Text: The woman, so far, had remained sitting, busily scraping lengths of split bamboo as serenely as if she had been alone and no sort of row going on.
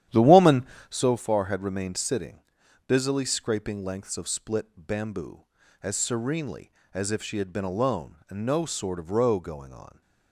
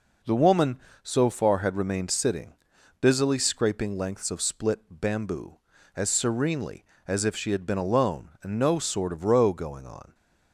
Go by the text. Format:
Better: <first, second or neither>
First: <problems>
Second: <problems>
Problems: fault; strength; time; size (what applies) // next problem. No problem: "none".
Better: second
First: starts louder than the rest; strong; until 1.1 s; 11 dB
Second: none